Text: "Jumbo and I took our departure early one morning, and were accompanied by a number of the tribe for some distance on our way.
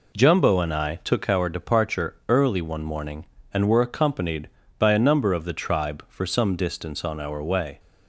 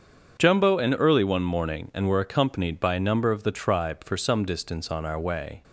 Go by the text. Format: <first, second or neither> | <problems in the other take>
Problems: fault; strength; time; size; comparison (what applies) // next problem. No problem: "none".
first | starts louder than the rest; strong; until 1.4 s; 7.5 dB // skips "I took our departure"; at 0.9 s